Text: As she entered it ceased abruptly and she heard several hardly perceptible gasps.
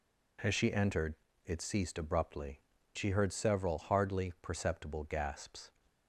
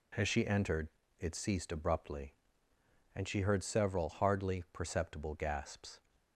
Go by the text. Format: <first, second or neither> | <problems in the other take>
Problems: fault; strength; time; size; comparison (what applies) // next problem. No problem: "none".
second | pauses between "entered" and "it"; slight; at 1.1 s; 0.30 s long; slight in the second // skips "and"; at 2.7 s